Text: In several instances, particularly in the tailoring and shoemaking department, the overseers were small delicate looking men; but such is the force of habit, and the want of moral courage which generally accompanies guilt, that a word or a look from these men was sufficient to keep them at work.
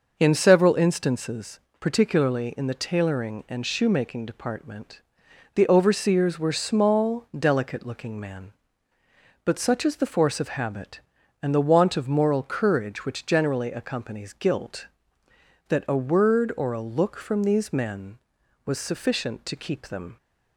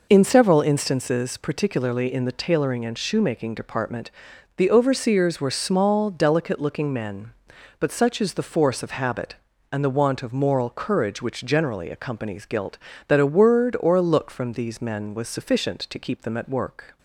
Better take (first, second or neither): second